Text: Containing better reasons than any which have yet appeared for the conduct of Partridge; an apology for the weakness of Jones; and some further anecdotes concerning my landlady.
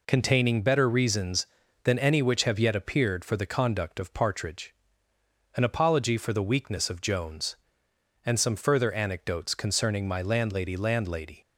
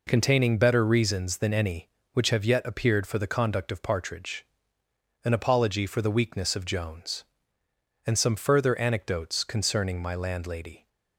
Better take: second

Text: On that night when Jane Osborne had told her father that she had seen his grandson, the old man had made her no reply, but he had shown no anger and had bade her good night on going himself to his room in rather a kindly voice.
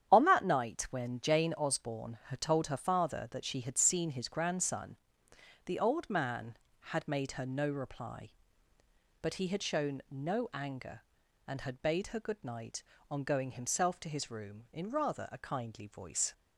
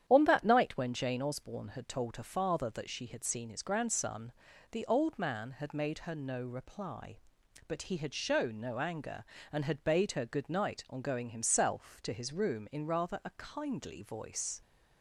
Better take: neither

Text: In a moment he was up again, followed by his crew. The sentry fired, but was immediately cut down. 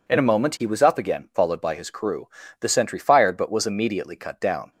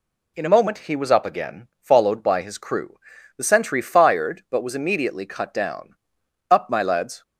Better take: first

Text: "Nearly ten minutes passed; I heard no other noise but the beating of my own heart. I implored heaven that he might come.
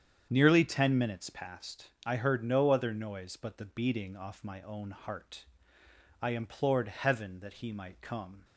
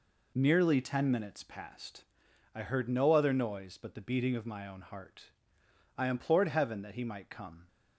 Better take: second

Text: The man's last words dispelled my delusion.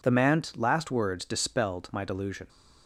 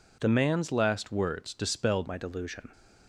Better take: first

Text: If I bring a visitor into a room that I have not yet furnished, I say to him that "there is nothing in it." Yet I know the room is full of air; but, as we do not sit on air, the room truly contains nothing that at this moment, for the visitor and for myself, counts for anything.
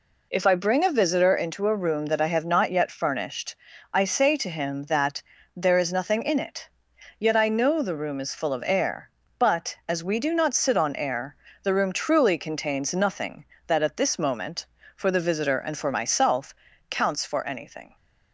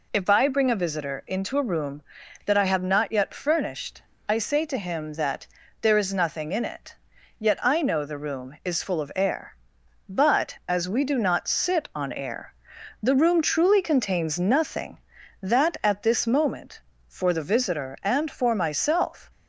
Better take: first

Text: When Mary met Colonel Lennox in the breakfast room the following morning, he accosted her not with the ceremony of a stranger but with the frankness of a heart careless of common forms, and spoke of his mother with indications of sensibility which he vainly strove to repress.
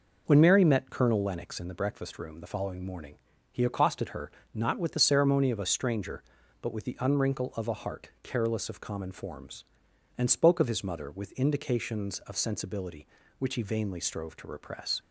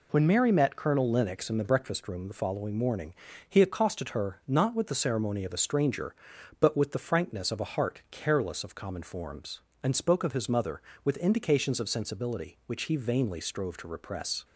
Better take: second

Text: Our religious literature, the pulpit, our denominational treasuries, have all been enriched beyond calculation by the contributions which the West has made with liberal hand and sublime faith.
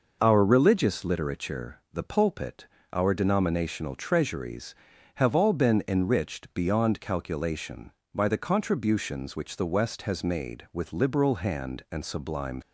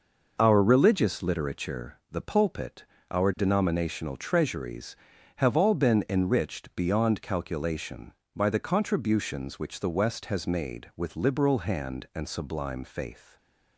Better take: second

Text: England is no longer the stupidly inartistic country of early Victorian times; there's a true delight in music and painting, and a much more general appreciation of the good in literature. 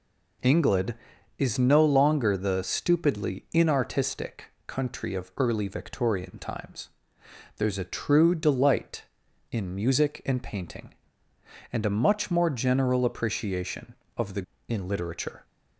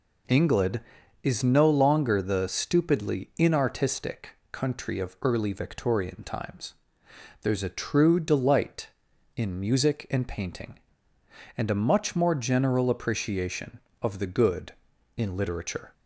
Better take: second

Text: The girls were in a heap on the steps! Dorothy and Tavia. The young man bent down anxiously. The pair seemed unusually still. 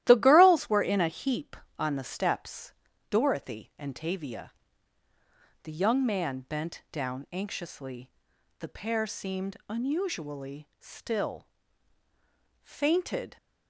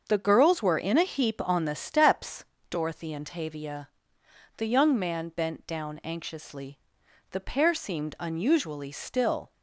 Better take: second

